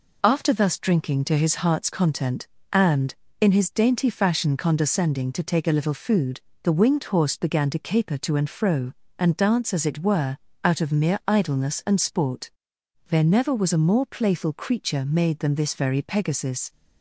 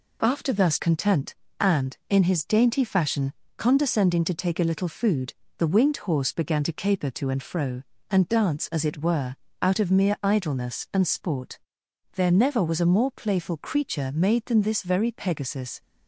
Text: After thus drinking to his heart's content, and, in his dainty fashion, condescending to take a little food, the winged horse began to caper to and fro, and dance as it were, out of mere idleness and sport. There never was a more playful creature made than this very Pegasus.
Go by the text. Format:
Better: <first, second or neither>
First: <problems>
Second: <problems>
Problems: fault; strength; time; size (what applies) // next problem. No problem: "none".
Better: first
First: none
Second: skips "drinking to his heart's"; at 0.7 s